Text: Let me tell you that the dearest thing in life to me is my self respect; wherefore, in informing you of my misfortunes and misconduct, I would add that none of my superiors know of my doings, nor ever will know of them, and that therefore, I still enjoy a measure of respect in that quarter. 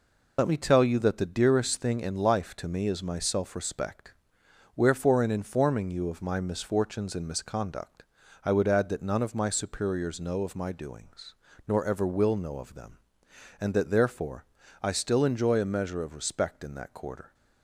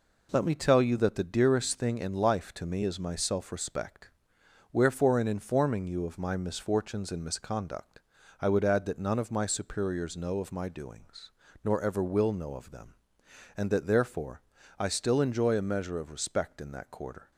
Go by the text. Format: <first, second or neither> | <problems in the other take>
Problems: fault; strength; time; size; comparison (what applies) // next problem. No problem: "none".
second | loses the start of "Let"; at 0.3 s; 60 ms